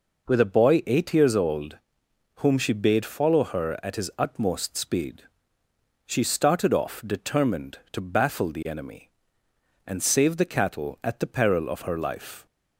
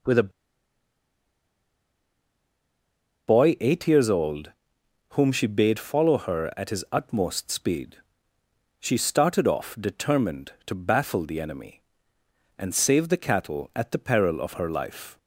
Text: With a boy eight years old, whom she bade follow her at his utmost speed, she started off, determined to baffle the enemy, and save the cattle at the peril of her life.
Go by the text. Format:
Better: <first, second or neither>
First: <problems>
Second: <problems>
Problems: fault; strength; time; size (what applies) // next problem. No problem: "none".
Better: first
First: none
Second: pauses between "a" and "boy"; strong; at 0.2 s; 2.9 s long